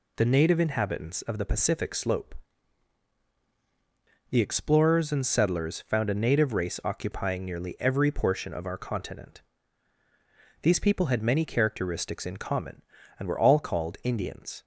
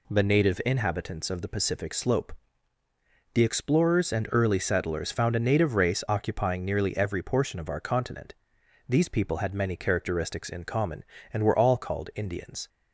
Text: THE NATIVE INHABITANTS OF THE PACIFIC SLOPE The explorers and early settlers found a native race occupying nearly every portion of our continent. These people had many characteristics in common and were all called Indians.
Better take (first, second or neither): second